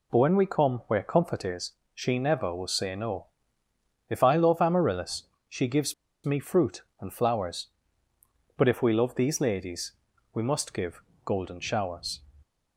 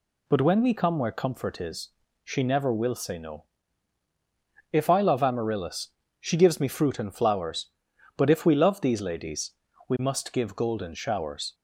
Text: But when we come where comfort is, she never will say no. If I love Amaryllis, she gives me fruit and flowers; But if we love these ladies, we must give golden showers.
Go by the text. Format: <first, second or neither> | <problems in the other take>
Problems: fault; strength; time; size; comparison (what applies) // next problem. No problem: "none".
second | pauses between "gives" and "me"; slight; at 5.9 s; 0.31 s long // pauses between "give" and "golden"; slight; at 11.0 s; 0.24 s long